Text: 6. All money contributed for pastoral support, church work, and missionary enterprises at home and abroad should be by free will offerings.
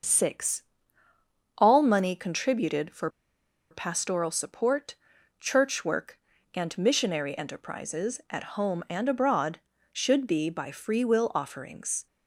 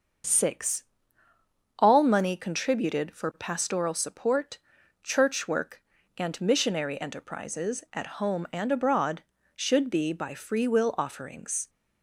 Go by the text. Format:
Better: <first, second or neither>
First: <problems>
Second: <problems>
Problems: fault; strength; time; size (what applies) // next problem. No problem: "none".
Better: second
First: starts louder than the rest; until 1.9 s; 6.5 dB // pauses between "for" and "pastoral"; noticeable; at 3.0 s; 0.62 s long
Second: starts louder than the rest; until 2.1 s; 6.5 dB